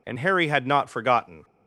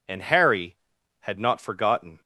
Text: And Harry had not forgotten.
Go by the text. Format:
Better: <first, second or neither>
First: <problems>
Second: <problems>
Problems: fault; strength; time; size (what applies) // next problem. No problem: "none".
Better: neither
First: none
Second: none